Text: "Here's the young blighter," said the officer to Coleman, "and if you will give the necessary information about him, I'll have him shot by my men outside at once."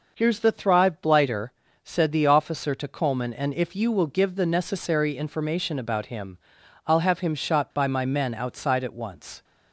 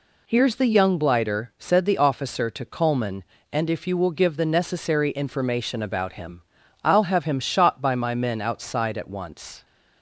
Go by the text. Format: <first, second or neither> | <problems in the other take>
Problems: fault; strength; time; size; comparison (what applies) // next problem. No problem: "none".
second | says "thrive" for "young"; at 0.5 s